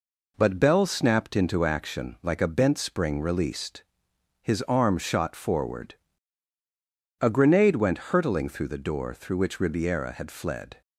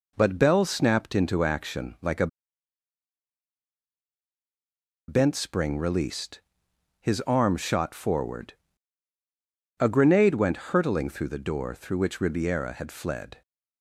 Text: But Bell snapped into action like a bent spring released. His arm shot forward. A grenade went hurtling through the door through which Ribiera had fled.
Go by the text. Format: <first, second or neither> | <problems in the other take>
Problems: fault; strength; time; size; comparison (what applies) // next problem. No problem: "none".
first | pauses between "a" and "bent"; strong; at 2.2 s; 2.8 s long